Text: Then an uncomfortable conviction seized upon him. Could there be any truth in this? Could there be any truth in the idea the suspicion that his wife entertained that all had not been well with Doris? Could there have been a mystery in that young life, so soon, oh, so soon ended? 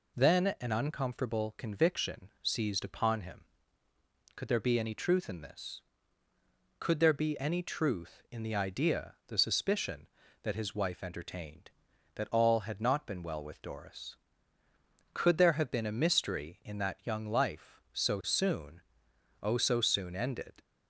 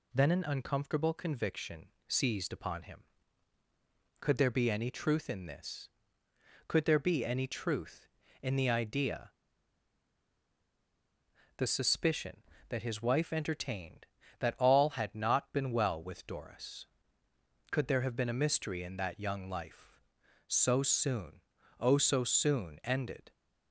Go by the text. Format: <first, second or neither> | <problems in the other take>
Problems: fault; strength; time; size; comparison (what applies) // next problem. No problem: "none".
first | pauses between "conviction" and "seized"; slight; at 1.8 s; 0.22 s long // pauses between "idea" and "the"; strong; at 9.3 s; 2.2 s long